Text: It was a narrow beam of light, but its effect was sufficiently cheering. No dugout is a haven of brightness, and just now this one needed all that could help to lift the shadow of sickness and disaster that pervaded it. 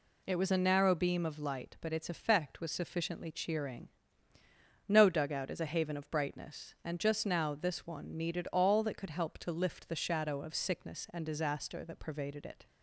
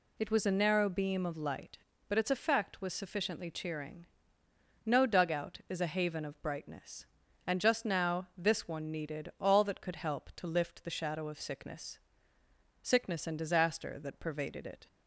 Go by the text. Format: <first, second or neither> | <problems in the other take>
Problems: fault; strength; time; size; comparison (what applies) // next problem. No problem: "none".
first | says "sickness" twice; at 12.8 s